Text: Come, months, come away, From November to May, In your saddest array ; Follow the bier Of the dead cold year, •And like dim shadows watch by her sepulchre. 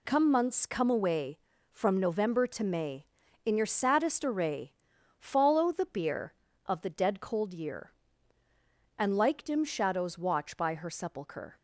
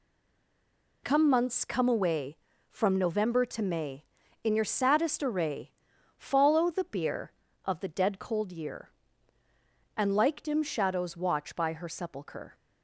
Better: first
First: none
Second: stays silent before the first word; until 1.0 s; 1.0 s long

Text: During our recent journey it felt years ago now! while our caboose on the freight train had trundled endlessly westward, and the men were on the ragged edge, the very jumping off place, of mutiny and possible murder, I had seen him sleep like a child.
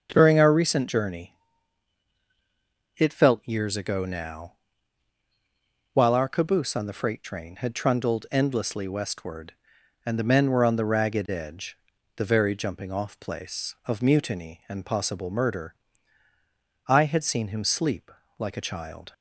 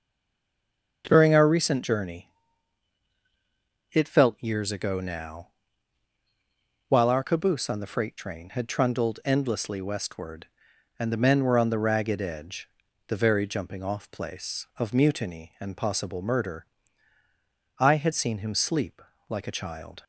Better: first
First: starts louder than the rest; until 1.1 s; 7 dB // pauses between "journey" and "it"; strong; at 1.3 s; 1.6 s long // pauses between "sleep" and "like"; slight; at 18.1 s; 0.26 s long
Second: stays silent before the first word; until 1.0 s; 1.0 s long // starts louder than the rest; until 2.0 s; 7 dB // pauses between "journey" and "it"; strong; at 2.2 s; 1.6 s long // pauses between "sleep" and "like"; slight; at 19.0 s; 0.26 s long

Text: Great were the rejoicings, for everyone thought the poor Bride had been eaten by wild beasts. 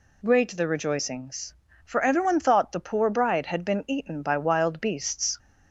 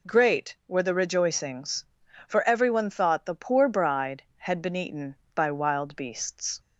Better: second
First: skips "were"; at 0.5 s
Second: none

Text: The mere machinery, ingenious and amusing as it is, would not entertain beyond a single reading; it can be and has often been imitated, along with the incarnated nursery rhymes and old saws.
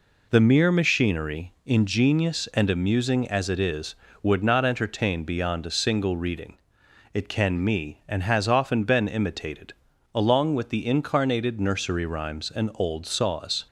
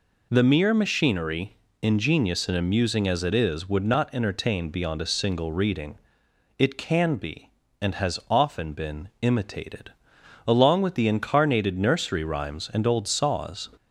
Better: second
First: says "me" for "be"; at 7.6 s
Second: none

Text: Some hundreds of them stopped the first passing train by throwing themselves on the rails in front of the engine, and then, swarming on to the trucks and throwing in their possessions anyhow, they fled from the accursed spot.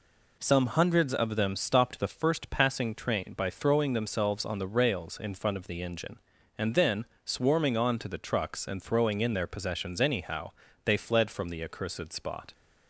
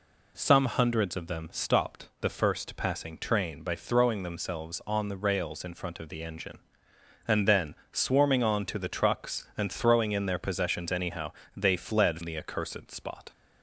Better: first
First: none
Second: skips "from"; at 12.2 s

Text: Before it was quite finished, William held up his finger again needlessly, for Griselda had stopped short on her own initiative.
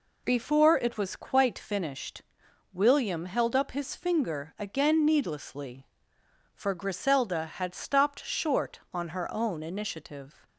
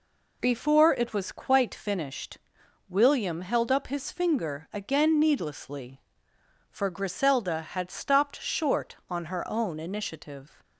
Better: neither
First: none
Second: none

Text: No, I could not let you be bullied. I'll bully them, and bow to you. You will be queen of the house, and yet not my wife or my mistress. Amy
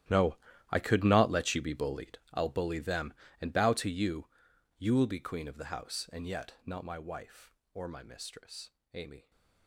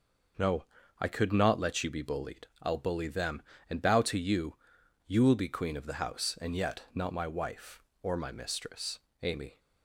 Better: second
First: gets quieter; strong; throughout; 17.5 dB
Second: none

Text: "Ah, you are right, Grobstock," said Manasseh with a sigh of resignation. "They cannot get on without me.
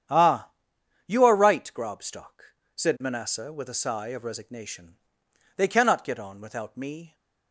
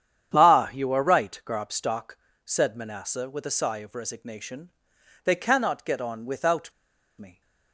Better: first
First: starts louder than the rest; strong; until 1.6 s; 9 dB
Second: starts louder than the rest; strong; until 1.3 s; 9 dB // pauses between "without" and "me"; noticeable; at 6.7 s; 0.46 s long

